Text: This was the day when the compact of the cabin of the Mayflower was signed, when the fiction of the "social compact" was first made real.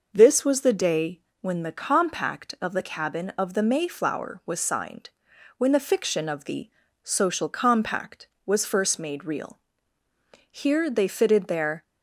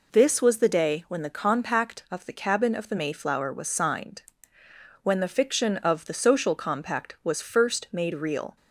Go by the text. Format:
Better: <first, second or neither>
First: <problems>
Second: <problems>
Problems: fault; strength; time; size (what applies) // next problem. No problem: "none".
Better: second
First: pauses between "day" and "when"; slight; at 1.1 s; 0.20 s long // pauses between "the" and "social"; slight; at 6.6 s; 0.36 s long // goes on to say "Here they fitted their"; from 10.4 s on; 1.3 s long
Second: none